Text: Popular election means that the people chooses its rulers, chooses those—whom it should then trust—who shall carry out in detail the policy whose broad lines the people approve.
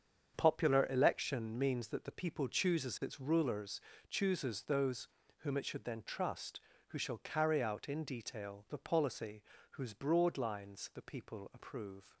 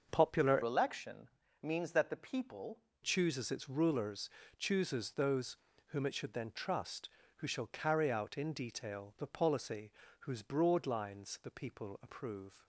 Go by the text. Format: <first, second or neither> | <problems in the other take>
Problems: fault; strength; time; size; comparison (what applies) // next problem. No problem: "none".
first | starts louder than the rest; until 1.1 s; 6.5 dB; strong in the first // changes voice from "election" to "people"; from 0.6 to 2.8 s; 2.2 s long // pauses between "election" and "means"; slight; at 1.2 s; 0.32 s long // pauses between "policy" and "whose"; slight; at 9.9 s; 0.28 s long; slight in the first